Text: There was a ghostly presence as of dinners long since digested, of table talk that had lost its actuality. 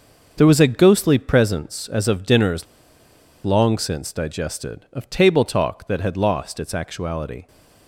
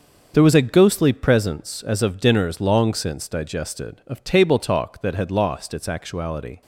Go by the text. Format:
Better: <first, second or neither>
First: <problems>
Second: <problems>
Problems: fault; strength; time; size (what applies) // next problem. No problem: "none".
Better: second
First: starts louder than the rest; until 1.3 s; 6.5 dB // pauses between "dinners" and "long"; noticeable; at 2.6 s; 0.79 s long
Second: starts louder than the rest; until 1.3 s; 6.5 dB